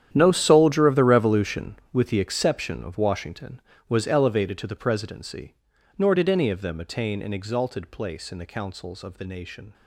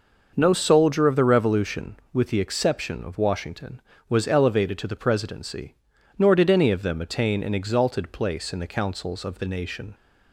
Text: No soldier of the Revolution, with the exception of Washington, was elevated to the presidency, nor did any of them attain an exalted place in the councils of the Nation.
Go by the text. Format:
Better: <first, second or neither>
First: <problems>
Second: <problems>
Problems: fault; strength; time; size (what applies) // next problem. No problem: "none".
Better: second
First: gets quieter; strong; throughout; 16 dB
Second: none